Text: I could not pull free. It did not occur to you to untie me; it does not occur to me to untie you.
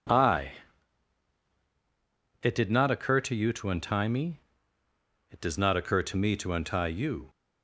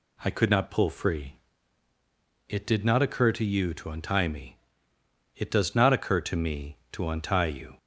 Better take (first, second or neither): second